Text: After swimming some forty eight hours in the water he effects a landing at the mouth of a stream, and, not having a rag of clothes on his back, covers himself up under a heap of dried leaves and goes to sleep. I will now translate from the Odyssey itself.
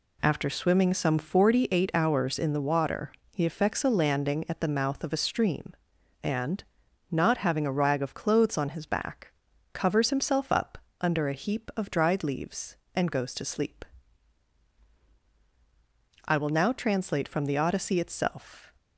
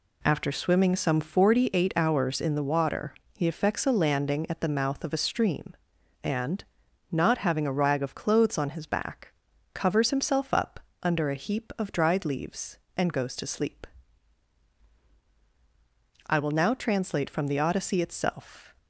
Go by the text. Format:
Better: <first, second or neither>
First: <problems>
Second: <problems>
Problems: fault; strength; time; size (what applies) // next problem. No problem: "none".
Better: neither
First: pauses between "water" and "he"; slight; at 3.1 s; 0.22 s long // pauses between "up" and "under"; slight; at 10.7 s; 0.24 s long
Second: pauses between "water" and "he"; slight; at 3.1 s; 0.22 s long // pauses between "up" and "under"; slight; at 10.7 s; 0.24 s long